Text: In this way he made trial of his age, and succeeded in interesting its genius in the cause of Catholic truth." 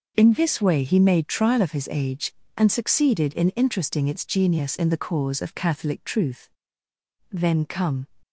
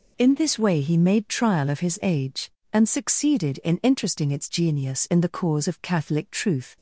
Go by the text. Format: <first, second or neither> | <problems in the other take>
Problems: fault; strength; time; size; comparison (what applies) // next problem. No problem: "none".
second | goes on to say "Then come"; noticeable; from 7.3 s on; 0.76 s long